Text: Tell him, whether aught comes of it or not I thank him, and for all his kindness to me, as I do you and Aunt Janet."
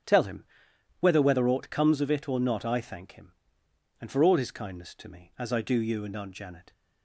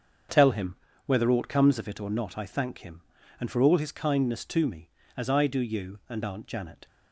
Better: second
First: starts louder than the rest; strong; until 1.6 s; 9.5 dB // says "whether" twice; at 1.2 s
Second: starts louder than the rest; until 1.5 s; 6.5 dB

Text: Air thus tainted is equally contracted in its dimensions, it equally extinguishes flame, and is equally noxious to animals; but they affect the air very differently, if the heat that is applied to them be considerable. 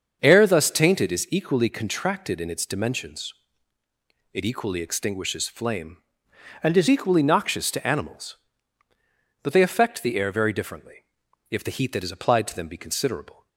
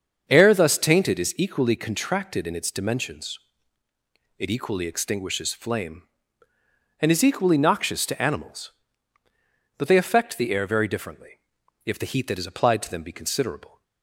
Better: second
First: starts louder than the rest; until 1.2 s; 6.5 dB // changes voice from "and" to "is"; from 6.6 to 6.8 s; 0.2 s long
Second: starts louder than the rest; until 1.2 s; 7 dB

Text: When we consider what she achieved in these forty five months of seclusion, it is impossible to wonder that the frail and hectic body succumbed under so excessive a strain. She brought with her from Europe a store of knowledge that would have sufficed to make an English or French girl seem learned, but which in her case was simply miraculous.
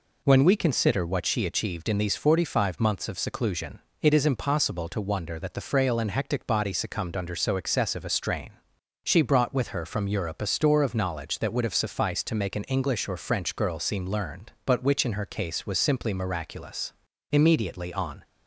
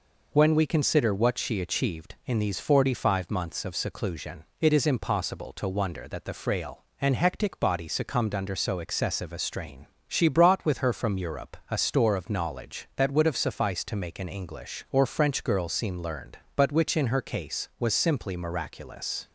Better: second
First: goes on to say "Immediately on"; noticeable; from 17.3 s on; 0.90 s long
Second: none

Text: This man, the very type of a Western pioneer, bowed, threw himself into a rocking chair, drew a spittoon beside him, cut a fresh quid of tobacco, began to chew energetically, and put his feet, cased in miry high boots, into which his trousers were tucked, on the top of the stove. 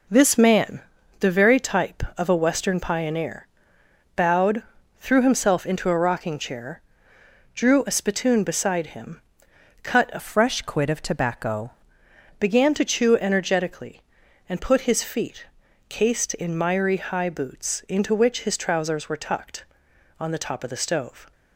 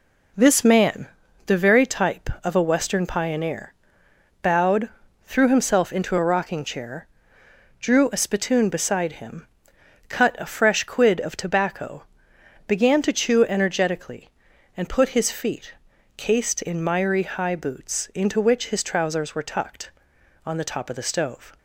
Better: second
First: changes voice from "fresh" to "tobacco"; from 10.1 to 11.7 s; 1.6 s long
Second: none

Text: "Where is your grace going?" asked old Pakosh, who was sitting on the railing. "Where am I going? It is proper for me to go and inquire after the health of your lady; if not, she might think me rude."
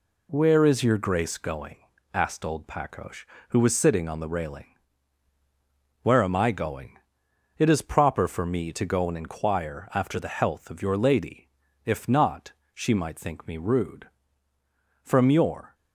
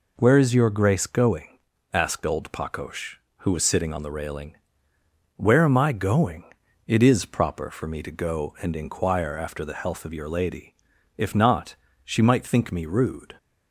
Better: second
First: goes on to say "From your"; noticeable; from 15.0 s on; 0.72 s long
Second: none

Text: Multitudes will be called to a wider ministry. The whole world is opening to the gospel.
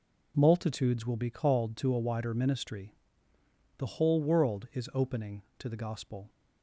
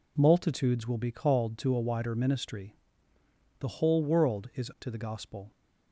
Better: first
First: none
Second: skips "opening"; at 4.7 s

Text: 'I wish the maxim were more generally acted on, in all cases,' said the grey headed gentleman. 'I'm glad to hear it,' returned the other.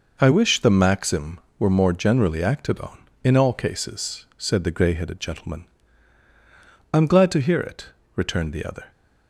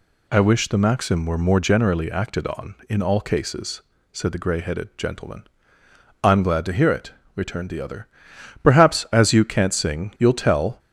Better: first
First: none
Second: goes on to say "Perhaps as you can't sing you'll tell"; strong; from 8.6 s on; 2.1 s long

